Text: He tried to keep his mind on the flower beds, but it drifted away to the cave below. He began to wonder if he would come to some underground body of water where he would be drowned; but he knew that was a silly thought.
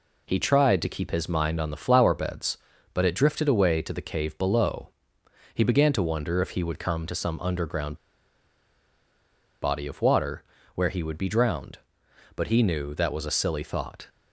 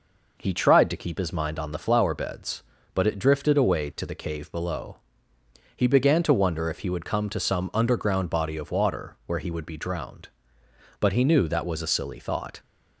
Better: second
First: pauses between "underground" and "body"; strong; at 7.9 s; 1.6 s long // pauses between "water" and "where"; slight; at 10.4 s; 0.30 s long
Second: none

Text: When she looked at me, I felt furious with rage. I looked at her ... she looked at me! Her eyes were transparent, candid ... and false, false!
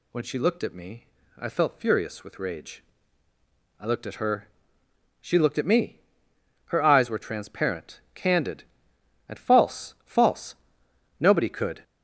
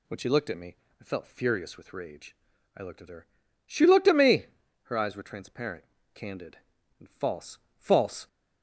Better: second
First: goes on to say "Nobody could"; noticeable; from 11.2 s on; 0.62 s long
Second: none

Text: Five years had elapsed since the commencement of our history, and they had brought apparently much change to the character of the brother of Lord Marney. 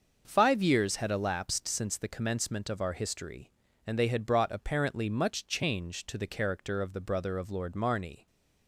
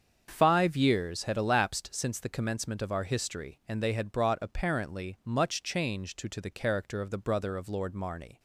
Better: first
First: starts louder than the rest; until 1.2 s; 6.5 dB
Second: starts louder than the rest; strong; until 1.3 s; 7 dB // says "to" twice; at 6.2 s

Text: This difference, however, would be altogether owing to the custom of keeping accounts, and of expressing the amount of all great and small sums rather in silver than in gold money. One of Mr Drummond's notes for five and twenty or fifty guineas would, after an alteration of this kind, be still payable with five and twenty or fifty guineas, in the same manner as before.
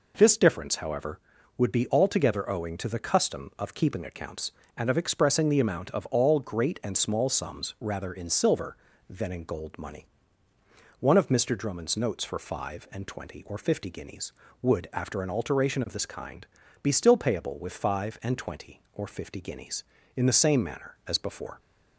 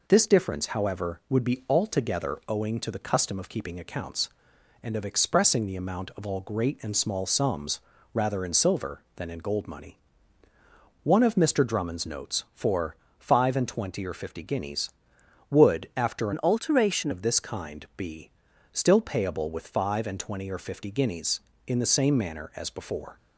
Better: first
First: none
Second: pauses between "sums" and "rather"; slight; at 7.7 s; 0.34 s long // pauses between "for" and "five"; slight; at 12.9 s; 0.22 s long // changes voice from "an" to "alteration"; from 16.3 to 17.1 s; 0.8 s long // pauses between "be" and "still"; at 18.2 s; 0.42 s long

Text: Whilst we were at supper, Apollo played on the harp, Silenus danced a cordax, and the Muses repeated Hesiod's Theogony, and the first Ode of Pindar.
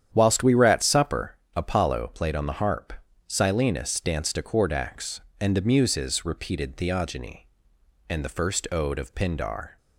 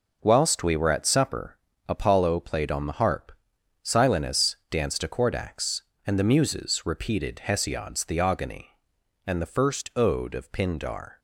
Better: second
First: starts louder than the rest; strong; until 1.1 s; 9.5 dB // skips "Hesiod's"; at 6.7 s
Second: none

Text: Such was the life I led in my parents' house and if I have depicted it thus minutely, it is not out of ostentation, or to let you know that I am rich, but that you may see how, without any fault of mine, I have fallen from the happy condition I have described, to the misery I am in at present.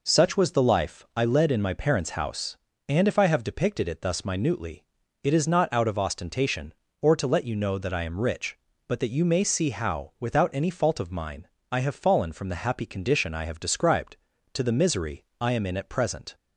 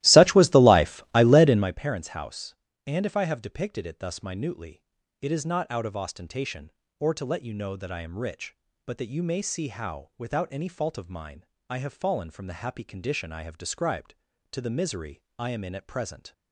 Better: first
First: pauses between "misery" and "I"; slight; at 15.2 s; 0.18 s long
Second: starts louder than the rest; strong; until 1.8 s; 16.5 dB // pauses between "misery" and "I"; slight; at 15.2 s; 0.18 s long

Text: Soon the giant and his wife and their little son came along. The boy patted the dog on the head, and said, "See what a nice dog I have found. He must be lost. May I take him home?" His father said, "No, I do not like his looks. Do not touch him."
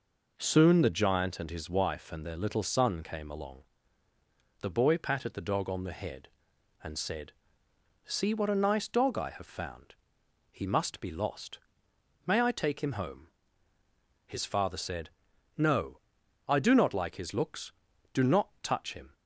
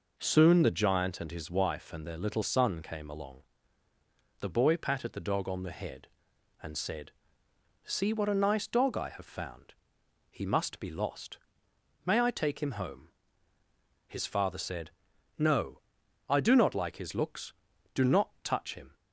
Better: neither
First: none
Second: none

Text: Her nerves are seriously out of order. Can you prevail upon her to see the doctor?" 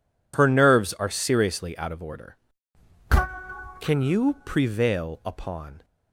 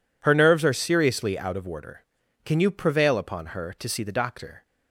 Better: second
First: stops before "her to see the doctor"; at 5.8 s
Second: none

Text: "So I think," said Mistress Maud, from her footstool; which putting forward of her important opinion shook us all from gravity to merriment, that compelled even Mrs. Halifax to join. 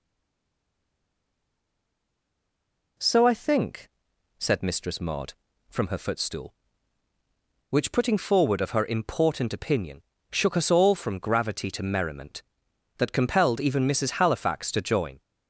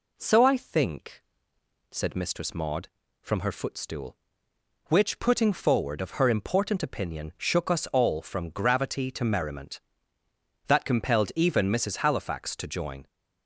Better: second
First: stays silent before the first word; strong; until 2.9 s; 2.9 s long // pauses between "opinion" and "shook"; slight; at 10.0 s; 0.30 s long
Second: none

